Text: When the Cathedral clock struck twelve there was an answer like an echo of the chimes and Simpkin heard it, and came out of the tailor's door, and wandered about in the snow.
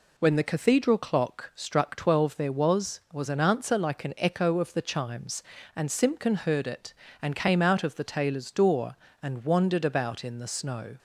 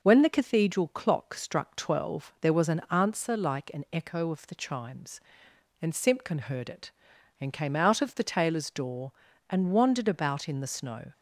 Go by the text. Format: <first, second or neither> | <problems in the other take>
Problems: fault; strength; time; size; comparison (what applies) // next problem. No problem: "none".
second | says "was" twice; at 3.1 s